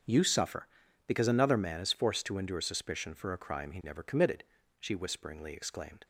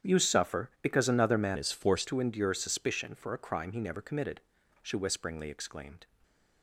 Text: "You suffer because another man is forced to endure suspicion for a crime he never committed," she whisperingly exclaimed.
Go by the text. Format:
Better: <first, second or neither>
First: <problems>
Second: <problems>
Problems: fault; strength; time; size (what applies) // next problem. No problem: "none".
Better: first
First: starts louder than the rest; until 1.4 s; 7 dB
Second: starts louder than the rest; strong; until 1.1 s; 9 dB // changes voice from "is" to "forced"; from 1.5 to 2.0 s; 0.5 s long